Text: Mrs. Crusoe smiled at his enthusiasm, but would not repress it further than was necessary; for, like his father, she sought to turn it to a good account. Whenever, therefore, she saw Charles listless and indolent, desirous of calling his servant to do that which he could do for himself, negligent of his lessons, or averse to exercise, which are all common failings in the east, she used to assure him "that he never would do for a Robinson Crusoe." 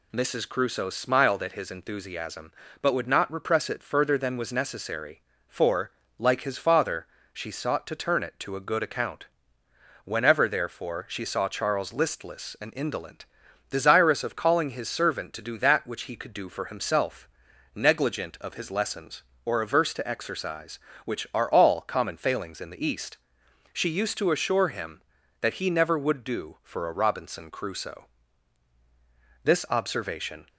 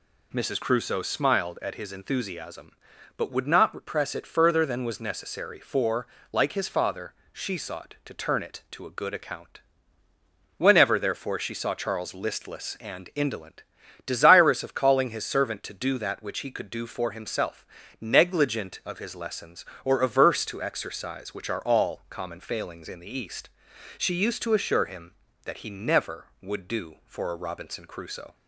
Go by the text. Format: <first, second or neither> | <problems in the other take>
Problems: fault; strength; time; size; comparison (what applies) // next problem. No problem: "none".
second | goes on to say "This observation"; noticeable; from 29.4 s on; 1.0 s long